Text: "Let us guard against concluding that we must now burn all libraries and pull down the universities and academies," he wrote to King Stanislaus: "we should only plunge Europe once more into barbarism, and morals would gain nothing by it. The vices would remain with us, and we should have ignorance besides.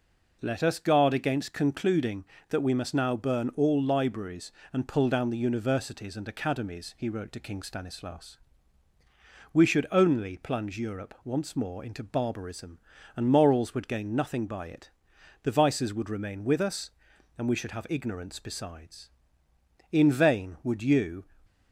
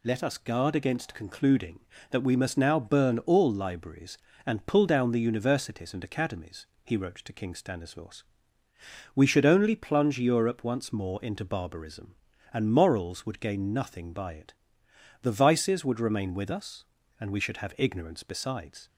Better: second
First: goes on to say "In vain would you"; from 19.8 s on; 1.3 s long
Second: none

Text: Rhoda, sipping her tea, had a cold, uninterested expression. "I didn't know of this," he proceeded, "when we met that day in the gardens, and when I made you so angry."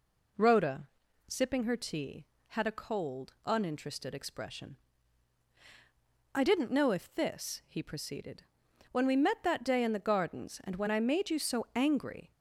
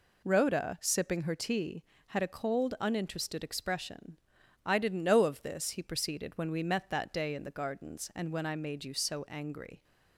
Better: second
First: says "if" for "of"; at 6.9 s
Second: none

